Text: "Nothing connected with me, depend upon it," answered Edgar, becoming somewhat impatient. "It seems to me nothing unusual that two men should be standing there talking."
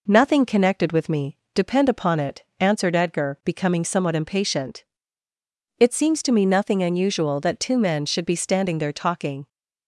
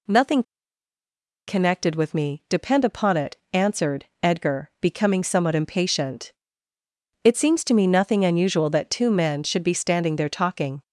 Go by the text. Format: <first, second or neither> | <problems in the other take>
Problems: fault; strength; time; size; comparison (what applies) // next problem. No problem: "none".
first | pauses between "Nothing" and "connected"; at 0.4 s; 1.0 s long // pauses between "answered" and "Edgar"; slight; at 4.0 s; 0.18 s long